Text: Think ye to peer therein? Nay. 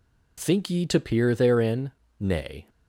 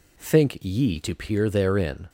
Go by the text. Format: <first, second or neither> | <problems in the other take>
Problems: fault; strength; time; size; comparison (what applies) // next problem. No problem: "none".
first | stops before "Nay"; at 2.0 s